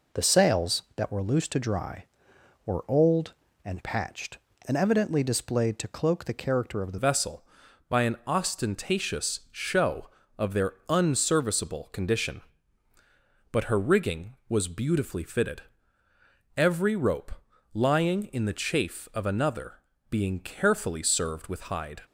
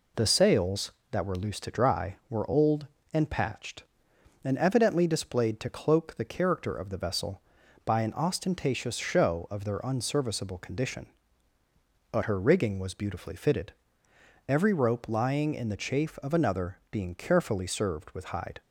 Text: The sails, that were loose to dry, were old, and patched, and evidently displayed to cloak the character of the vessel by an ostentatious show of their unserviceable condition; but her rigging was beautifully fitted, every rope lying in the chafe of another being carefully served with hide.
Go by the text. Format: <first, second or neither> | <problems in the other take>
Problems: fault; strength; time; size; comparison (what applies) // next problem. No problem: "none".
second | changes voice at "vessel"; from 6.9 s on; 15.1 s long // pauses between "rope" and "lying"; at 17.3 s; 0.42 s long // pauses between "another" and "being"; slight; at 19.8 s; 0.28 s long